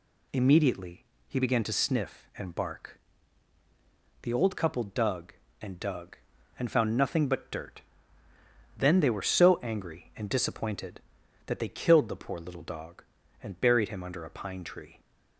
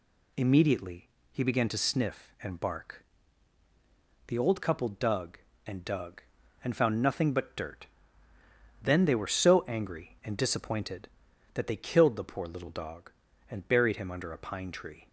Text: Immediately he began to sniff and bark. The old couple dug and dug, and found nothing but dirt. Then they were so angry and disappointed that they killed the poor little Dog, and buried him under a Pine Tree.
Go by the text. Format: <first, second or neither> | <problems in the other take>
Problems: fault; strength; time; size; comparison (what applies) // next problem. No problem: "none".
neither | pauses between "Immediately" and "he"; slight; the same in both